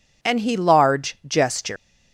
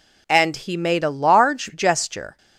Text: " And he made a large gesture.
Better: second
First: skips "made a"; at 0.5 s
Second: none

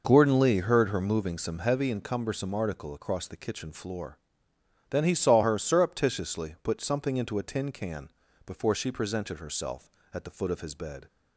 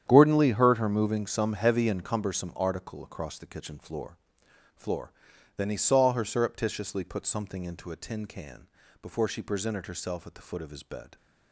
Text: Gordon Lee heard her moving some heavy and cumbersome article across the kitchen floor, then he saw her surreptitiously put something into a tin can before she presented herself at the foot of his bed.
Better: first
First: pauses between "can" and "before"; slight; at 8.1 s; 0.34 s long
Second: starts louder than the rest; strong; until 1.0 s; 9.5 dB // says "floor" twice; at 4.7 s // pauses between "can" and "before"; slight; at 8.6 s; 0.34 s long

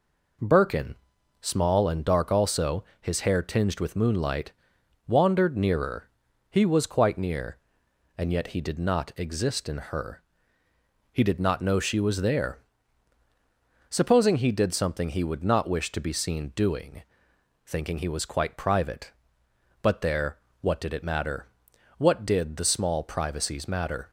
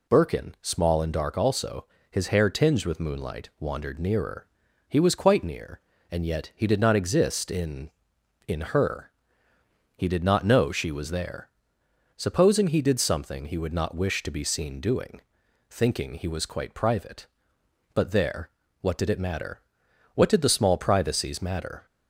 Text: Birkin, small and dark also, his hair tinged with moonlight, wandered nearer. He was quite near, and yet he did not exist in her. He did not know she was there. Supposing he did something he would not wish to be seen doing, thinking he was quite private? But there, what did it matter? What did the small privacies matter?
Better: first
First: none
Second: says "in" twice; at 8.4 s

